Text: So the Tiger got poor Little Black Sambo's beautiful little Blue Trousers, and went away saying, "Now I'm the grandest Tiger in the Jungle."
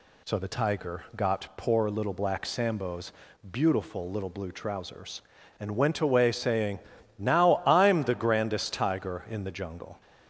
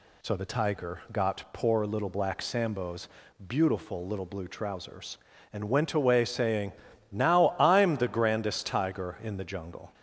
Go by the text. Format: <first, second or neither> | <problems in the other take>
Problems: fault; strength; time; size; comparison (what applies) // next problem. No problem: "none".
neither | pauses between "Sambo's" and "beautiful"; the same in both